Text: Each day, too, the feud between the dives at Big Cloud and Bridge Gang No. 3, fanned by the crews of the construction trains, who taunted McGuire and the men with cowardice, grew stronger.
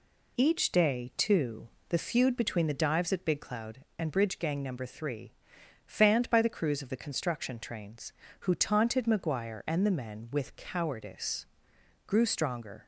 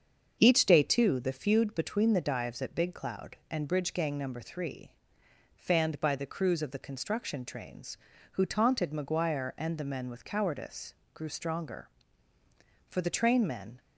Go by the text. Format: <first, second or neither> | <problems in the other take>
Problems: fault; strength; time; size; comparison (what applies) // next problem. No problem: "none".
first | starts louder than the rest; until 1.4 s; 7 dB // goes on to say "For the train men"; noticeable; from 12.8 s on; 0.92 s long